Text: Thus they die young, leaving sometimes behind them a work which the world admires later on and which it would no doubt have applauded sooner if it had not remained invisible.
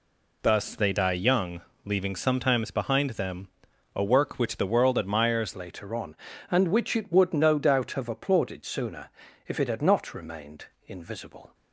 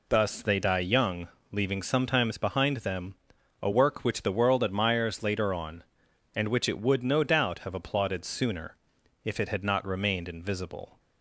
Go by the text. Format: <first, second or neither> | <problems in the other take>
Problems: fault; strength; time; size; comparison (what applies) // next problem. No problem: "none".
second | pauses between "them" and "a"; noticeable; at 3.4 s; 0.46 s long; noticeable in the second // changes voice at "later"; from 5.5 s on; 6.0 s long // pauses between "sooner" and "if"; at 9.0 s; 0.38 s long; noticeable in the second // pauses between "remained" and "invisible"; slight; at 10.6 s; 0.20 s long